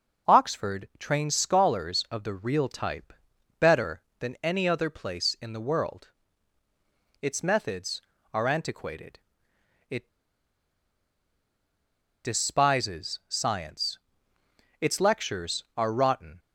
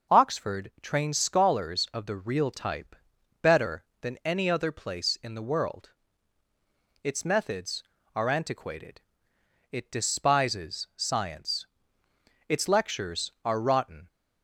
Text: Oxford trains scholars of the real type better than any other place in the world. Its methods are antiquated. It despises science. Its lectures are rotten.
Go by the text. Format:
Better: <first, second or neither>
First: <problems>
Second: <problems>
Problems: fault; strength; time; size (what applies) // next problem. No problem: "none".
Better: second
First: pauses between "type" and "better"; noticeable; at 3.1 s; 0.46 s long // pauses between "It" and "despises"; strong; at 10.0 s; 2.1 s long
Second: pauses between "type" and "better"; noticeable; at 2.9 s; 0.46 s long